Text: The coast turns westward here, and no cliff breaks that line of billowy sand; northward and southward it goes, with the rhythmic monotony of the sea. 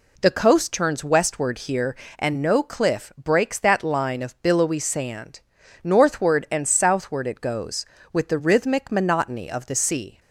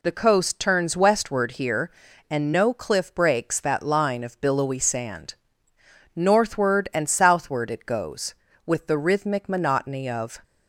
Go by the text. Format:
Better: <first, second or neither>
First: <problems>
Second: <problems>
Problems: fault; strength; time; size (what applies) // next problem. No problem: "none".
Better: first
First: none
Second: stops before "the sea"; at 10.4 s